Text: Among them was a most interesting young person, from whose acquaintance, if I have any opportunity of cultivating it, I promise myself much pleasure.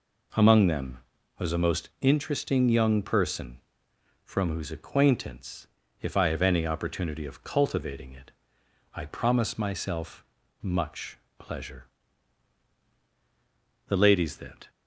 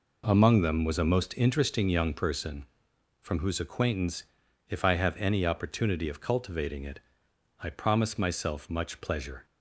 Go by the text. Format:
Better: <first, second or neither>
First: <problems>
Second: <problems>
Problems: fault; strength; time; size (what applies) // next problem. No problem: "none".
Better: second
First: pauses between "myself" and "much"; at 10.2 s; 0.38 s long // pauses between "much" and "pleasure"; slight; at 11.1 s; 0.24 s long // goes on to say "The ladies that"; noticeable; from 13.8 s on; 0.82 s long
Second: none